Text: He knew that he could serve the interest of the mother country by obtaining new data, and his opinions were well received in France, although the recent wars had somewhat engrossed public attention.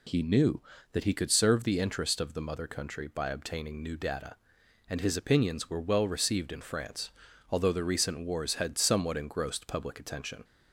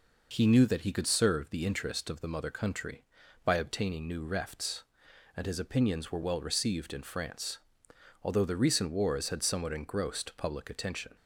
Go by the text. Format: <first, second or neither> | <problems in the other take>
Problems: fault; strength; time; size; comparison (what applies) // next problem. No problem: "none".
first | says "refts" for "data"; at 4.2 s